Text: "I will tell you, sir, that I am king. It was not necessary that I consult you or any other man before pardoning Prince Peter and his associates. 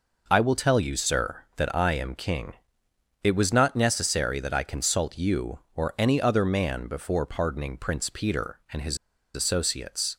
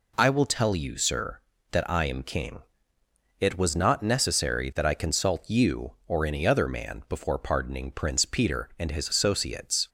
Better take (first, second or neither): second